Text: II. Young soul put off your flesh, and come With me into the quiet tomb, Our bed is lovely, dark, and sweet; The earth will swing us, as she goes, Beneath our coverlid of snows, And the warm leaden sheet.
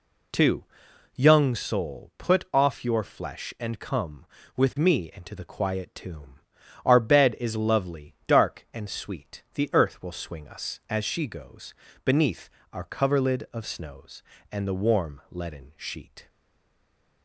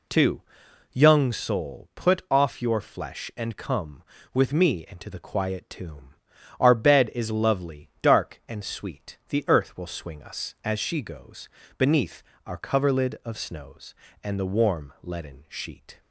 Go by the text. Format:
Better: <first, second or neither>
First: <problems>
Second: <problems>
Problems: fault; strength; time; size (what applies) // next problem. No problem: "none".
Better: second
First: pauses between "Beneath" and "our"; slight; at 12.4 s; 0.22 s long // stays silent after the last word; from 16.2 s on; 1.0 s long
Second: pauses between "Beneath" and "our"; slight; at 12.2 s; 0.22 s long